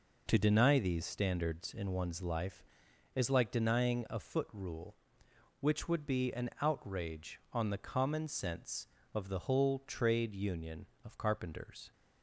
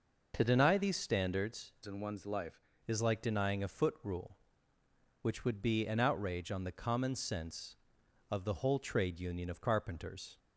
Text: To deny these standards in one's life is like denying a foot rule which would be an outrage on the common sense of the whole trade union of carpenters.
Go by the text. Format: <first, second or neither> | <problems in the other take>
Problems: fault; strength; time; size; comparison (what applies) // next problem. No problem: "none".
first | changes voice from "in" to "life"; from 1.8 to 2.6 s; 0.8 s long